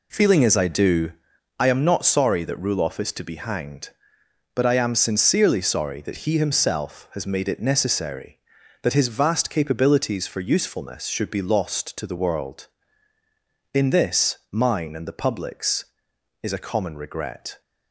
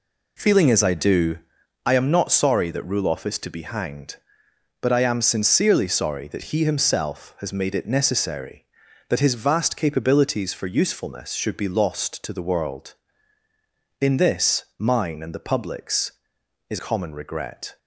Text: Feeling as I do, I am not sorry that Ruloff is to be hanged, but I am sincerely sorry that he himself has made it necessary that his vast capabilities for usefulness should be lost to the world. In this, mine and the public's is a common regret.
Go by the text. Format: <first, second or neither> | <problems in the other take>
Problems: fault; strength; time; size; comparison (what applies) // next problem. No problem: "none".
first | skips "a"; at 16.7 s